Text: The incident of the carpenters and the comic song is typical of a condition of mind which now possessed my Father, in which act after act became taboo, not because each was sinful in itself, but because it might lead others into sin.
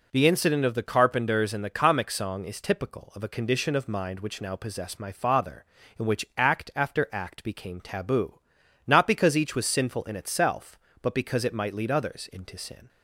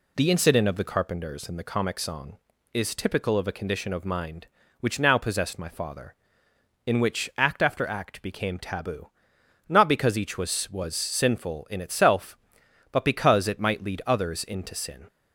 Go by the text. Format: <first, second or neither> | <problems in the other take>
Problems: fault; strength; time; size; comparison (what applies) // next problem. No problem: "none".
first | says "was" twice; at 10.7 s